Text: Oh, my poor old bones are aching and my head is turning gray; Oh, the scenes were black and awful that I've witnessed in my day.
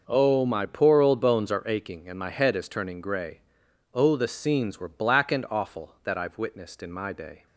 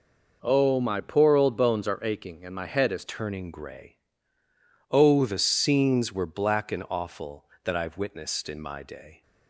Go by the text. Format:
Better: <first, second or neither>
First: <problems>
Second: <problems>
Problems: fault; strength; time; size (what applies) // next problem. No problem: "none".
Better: first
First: none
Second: changes voice at "turning"; from 3.0 s on; 6.2 s long